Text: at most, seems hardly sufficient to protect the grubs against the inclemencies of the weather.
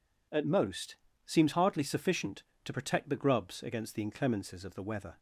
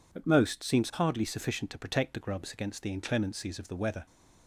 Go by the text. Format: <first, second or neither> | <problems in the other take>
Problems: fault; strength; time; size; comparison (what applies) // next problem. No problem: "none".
neither | none